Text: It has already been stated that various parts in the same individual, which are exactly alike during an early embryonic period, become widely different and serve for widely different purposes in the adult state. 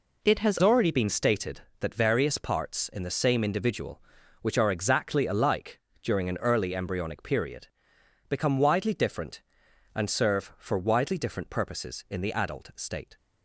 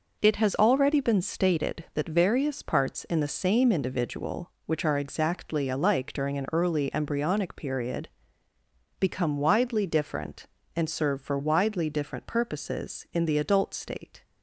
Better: second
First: changes voice at "already"; from 0.6 s on; 12.5 s long // pauses between "alike" and "during"; slight; at 5.7 s; 0.22 s long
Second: none

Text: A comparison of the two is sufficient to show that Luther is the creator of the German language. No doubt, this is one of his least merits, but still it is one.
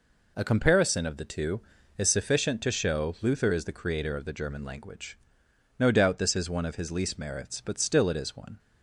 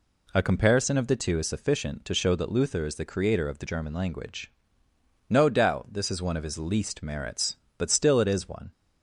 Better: second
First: skips "that"; at 3.1 s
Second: none

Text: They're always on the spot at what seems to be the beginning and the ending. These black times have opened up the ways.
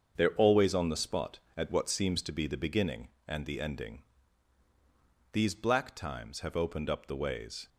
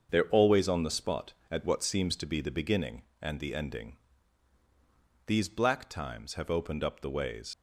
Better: first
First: starts louder than the rest; until 1.1 s; 7 dB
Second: starts louder than the rest; until 1.1 s; 6.5 dB // leaves "ways" unfinished; at 7.5 s; 90 ms

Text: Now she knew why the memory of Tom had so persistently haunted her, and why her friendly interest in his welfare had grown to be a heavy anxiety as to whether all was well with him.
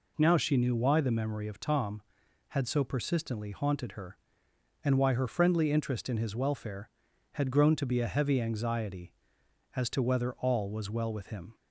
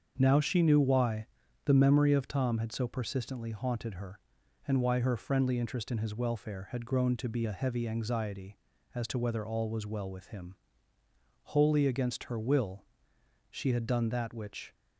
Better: first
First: none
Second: starts louder than the rest; until 1.1 s; 7 dB // pauses between "why" and "the"; at 1.2 s; 0.40 s long // goes on to say "Wholly against her will she had done that which"; strong; from 11.4 s on; 3.3 s long

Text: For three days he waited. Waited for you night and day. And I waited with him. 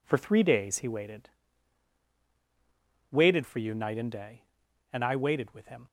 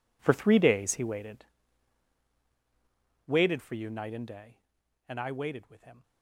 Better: first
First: none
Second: gets quieter; strong; throughout; 15 dB

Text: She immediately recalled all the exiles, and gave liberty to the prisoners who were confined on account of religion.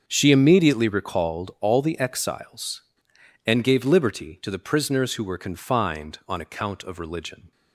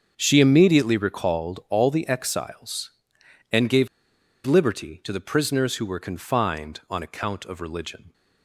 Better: first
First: starts louder than the rest; until 1.0 s; 6.5 dB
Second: starts louder than the rest; until 1.1 s; 6.5 dB // pauses between "gave" and "liberty"; noticeable; at 3.8 s; 0.58 s long

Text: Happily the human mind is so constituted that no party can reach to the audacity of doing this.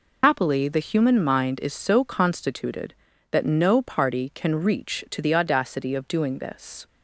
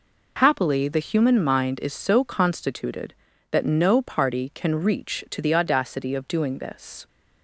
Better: second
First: loses the start of "Happily"; at 0.2 s; 70 ms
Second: none

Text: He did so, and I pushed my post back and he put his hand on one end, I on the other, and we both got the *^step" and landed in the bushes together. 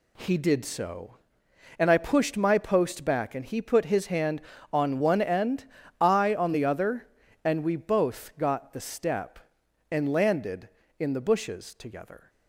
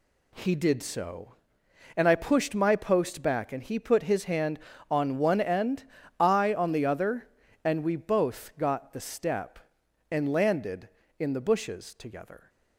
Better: neither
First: none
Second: none

